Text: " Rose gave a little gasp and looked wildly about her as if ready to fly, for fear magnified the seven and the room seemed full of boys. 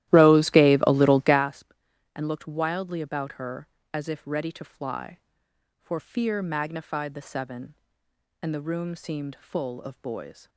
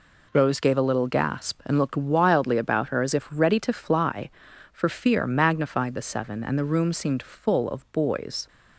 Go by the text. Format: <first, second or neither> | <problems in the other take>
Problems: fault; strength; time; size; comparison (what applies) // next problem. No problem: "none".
second | starts louder than the rest; strong; until 1.5 s; 14.5 dB